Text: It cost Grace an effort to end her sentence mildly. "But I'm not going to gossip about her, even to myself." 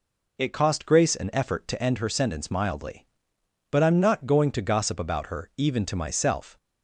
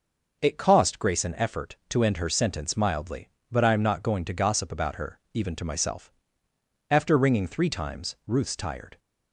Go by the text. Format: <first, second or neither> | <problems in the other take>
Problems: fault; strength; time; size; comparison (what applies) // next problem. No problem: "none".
first | goes on to say "After ringing three times Ruth's tired"; strong; from 6.8 s on; 2.1 s long